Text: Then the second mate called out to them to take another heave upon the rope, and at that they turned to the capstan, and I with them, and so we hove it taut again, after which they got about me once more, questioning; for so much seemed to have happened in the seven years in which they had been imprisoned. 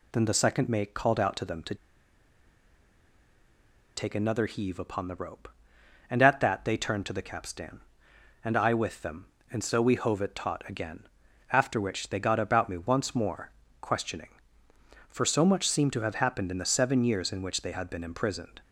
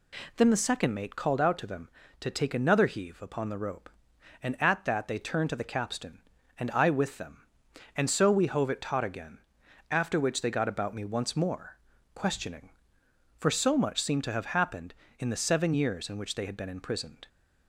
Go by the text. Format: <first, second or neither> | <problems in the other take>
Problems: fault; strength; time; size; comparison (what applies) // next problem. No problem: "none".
second | pauses between "to" and "take"; strong; at 1.7 s; 2.2 s long